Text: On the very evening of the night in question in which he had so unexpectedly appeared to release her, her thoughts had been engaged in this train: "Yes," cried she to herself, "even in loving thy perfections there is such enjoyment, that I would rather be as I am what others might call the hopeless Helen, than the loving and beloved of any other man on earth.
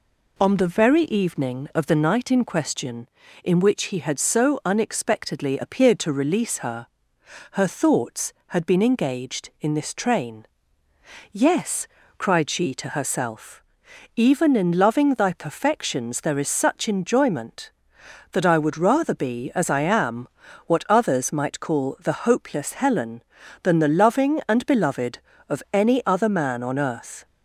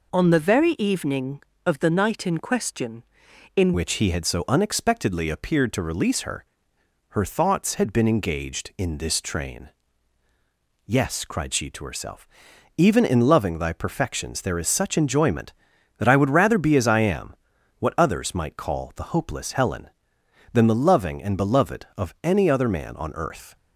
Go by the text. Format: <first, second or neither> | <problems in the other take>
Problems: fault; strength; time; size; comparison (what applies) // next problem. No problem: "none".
first | changes voice at "which"; from 3.7 s on; 19.8 s long // pauses between "am" and "what"; noticeable; at 17.3 s; 0.46 s long; also in the first